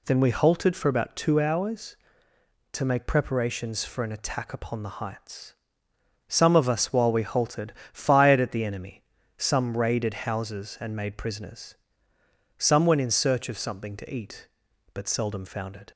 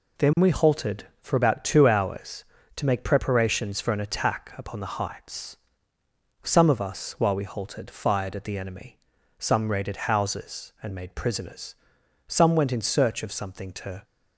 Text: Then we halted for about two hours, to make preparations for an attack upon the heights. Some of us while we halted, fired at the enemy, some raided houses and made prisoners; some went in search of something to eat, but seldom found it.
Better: first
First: none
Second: stops before "eat but seldom found it"; at 14.0 s

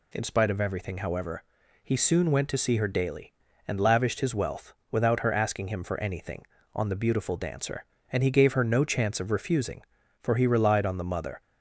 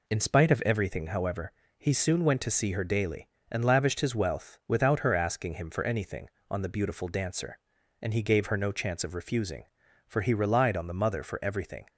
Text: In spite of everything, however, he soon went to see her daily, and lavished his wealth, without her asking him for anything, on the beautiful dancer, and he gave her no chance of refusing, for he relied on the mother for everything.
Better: second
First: stops before "for everything"; at 11.4 s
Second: none

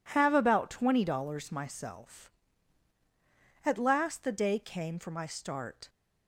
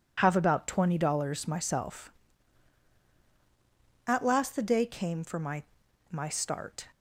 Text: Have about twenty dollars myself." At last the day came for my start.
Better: first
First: none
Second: says "my" twice; at 6.1 s

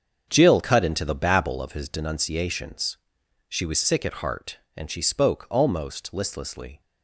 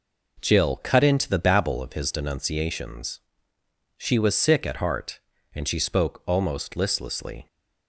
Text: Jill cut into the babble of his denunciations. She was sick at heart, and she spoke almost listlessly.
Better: second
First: starts louder than the rest; strong; until 1.8 s; 7 dB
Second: none

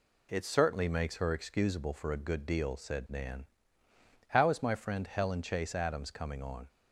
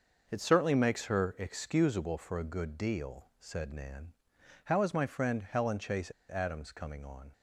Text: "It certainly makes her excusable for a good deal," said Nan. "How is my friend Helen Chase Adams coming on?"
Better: first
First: none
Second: starts louder than the rest; noticeable; until 1.2 s; 6 dB // pauses between "Chase" and "Adams"; slight; at 6.1 s; 0.18 s long

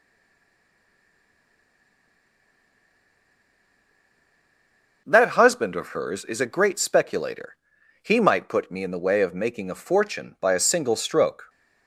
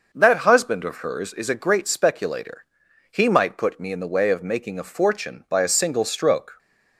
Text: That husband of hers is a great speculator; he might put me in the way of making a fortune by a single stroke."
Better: second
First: stays silent before the first word; strong; until 5.0 s; 5.0 s long // starts louder than the rest; noticeable; until 6.0 s; 6 dB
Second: starts louder than the rest; noticeable; until 1.1 s; 6 dB

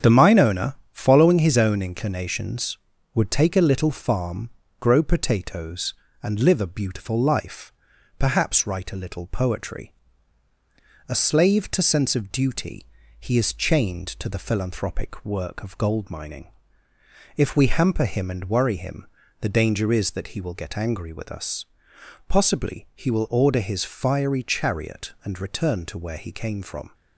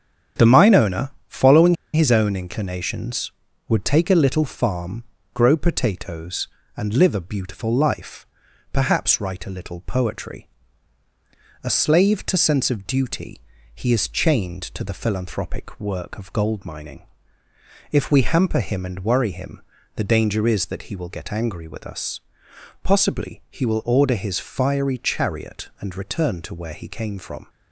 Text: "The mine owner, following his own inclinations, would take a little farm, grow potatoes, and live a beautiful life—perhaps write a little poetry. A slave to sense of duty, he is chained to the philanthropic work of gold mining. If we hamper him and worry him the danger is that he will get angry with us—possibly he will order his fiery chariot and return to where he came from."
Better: first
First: starts louder than the rest; strong; until 1.2 s; 8 dB // pauses between "him" and "the"; slight; at 19.0 s; 0.36 s long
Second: starts louder than the rest; strong; until 1.5 s; 8 dB // pauses between "following" and "his"; slight; at 1.7 s; 0.18 s long // pauses between "him" and "the"; slight; at 19.6 s; 0.36 s long

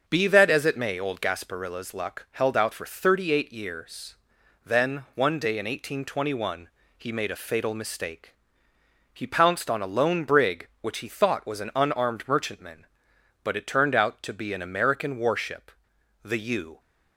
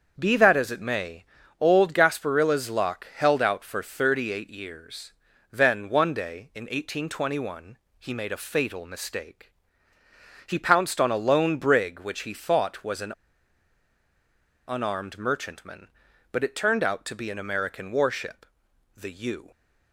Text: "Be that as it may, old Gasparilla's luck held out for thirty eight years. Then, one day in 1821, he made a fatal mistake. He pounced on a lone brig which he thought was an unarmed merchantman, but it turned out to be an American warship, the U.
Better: first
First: starts louder than the rest; until 1.1 s; 6.5 dB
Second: starts louder than the rest; until 1.2 s; 6.5 dB // pauses between "an" and "unarmed"; strong; at 13.1 s; 1.5 s long

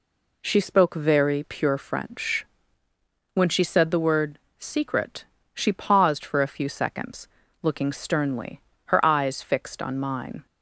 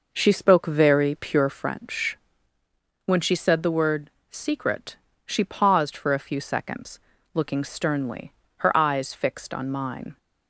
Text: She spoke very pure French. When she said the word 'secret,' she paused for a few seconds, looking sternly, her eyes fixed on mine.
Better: first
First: pauses between "word" and "secret"; slight; at 4.3 s; 0.20 s long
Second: starts louder than the rest; noticeable; until 1.7 s; 5.5 dB // pauses between "word" and "secret"; slight; at 4.0 s; 0.20 s long

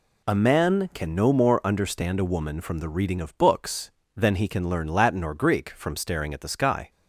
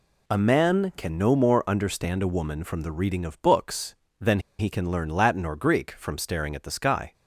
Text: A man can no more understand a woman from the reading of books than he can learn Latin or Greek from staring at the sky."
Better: first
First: none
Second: pauses between "than" and "he"; slight; at 4.3 s; 0.19 s long

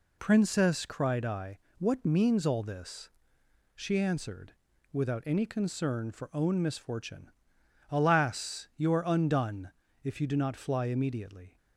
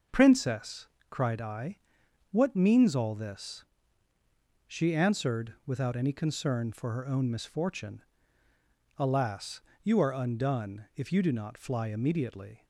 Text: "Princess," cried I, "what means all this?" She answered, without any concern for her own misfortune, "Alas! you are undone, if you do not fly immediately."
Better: second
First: skips "her"; at 6.3 s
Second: none

